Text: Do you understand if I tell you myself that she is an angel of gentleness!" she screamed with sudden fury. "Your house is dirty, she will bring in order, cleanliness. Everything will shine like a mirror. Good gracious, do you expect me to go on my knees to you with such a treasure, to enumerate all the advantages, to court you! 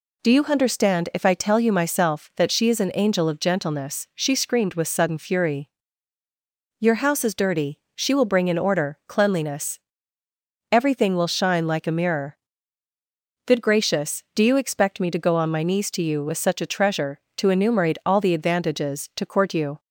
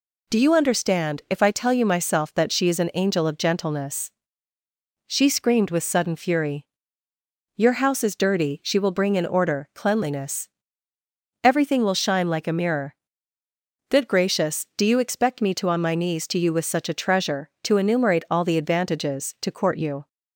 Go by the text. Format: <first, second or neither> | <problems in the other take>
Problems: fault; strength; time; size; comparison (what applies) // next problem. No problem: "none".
first | skips "go"; at 15.6 s